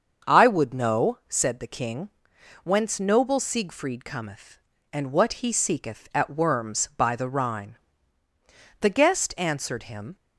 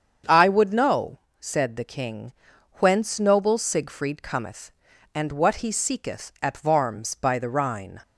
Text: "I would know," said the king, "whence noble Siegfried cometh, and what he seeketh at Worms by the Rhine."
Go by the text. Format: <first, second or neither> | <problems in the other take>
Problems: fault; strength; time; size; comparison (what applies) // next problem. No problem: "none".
second | starts louder than the rest; until 1.3 s; 6.5 dB; strong in the second // goes on to say "The guest answered him"; from 8.7 s on; 1.3 s long